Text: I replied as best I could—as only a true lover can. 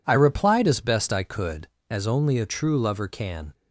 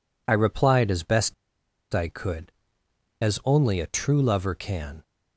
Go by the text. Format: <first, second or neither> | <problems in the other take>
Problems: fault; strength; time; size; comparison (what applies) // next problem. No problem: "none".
first | pauses between "best" and "I"; noticeable; at 1.3 s; 0.59 s long